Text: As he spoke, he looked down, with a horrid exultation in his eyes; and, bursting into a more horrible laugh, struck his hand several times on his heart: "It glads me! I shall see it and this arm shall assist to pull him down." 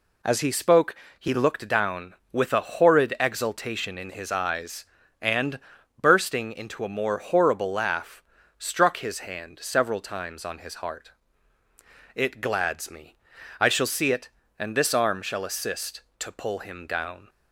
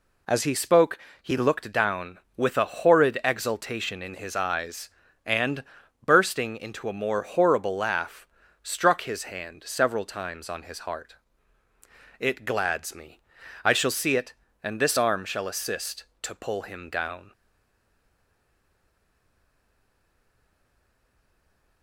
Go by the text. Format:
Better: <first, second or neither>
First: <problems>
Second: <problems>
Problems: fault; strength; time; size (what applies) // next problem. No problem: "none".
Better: first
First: none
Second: stays silent after the last word; strong; from 17.3 s on; 4.5 s long